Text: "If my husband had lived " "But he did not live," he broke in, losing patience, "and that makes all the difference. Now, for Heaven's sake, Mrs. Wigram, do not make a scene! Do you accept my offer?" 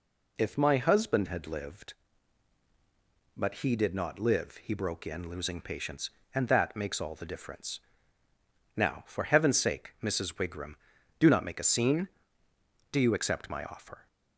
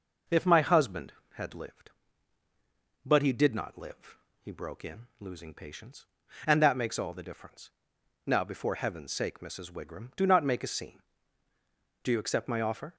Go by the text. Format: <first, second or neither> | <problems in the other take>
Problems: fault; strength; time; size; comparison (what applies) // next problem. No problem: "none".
first | says "before" for "for"; at 8.4 s